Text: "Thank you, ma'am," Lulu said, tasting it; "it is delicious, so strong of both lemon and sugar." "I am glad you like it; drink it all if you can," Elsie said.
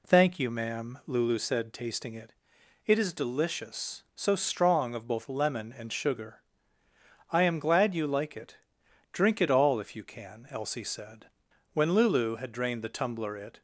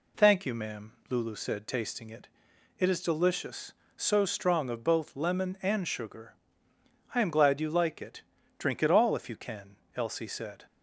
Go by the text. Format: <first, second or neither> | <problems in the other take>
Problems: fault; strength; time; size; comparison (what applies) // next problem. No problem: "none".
second | goes on to say "When Lulu had drained the tumbler it"; strong; from 11.7 s on; 1.8 s long